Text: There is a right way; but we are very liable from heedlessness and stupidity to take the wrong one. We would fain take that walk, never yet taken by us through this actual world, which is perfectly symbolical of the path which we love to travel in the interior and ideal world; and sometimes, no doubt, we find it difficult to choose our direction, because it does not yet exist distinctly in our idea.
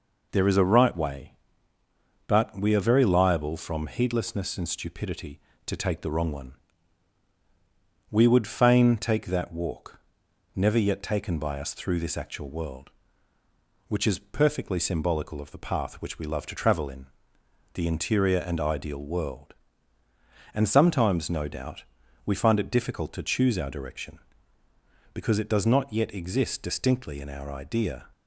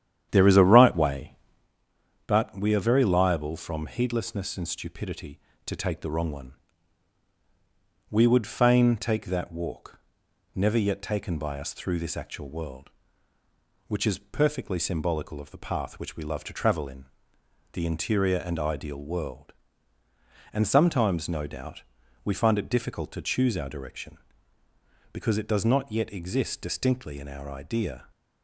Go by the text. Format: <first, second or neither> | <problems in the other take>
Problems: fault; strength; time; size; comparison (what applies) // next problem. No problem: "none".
first | starts louder than the rest; strong; until 1.7 s; 10 dB // pauses between "in" and "the"; noticeable; at 17.0 s; 0.68 s long; noticeable in the first